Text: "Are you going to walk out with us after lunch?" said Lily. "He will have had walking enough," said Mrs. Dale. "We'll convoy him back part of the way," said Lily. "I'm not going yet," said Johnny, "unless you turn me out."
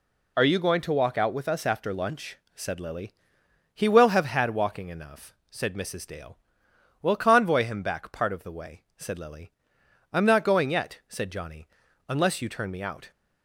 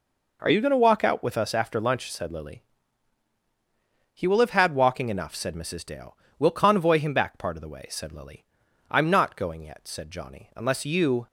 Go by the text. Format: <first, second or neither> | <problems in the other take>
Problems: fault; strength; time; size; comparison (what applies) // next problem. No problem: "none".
first | stops before "turn me out"; at 11.2 s